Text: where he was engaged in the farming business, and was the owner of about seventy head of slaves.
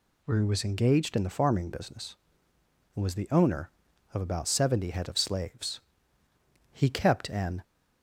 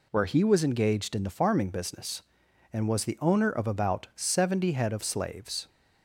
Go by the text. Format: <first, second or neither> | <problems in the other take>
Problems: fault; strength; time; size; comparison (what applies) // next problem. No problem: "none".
second | goes on to say "He kept an"; noticeable; from 6.7 s on; 0.92 s long